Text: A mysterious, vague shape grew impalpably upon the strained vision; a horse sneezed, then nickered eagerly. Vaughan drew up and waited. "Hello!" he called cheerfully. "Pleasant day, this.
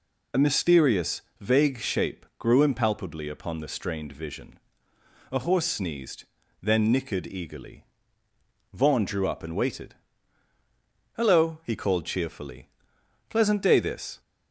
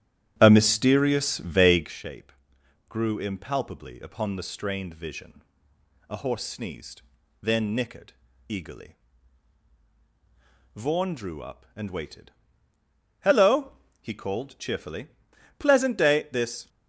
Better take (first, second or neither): first